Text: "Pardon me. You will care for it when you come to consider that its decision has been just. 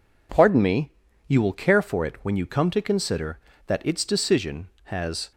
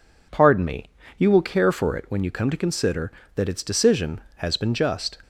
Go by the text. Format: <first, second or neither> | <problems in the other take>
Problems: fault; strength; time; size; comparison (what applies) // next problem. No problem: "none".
second | stops before "been just"; at 5.3 s